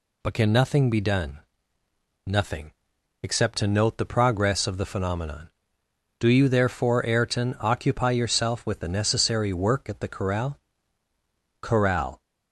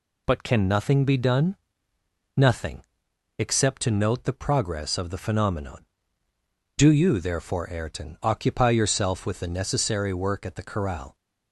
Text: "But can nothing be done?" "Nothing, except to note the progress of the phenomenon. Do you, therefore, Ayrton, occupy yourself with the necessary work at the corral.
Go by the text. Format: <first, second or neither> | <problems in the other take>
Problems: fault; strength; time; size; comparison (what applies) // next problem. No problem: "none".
second | says "corral" twice; at 11.6 s